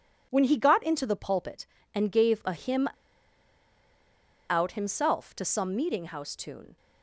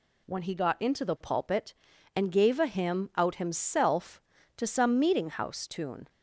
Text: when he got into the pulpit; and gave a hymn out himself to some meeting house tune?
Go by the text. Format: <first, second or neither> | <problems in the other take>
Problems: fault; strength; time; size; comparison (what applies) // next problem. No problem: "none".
second | pauses between "hymn" and "out"; strong; at 2.8 s; 1.6 s long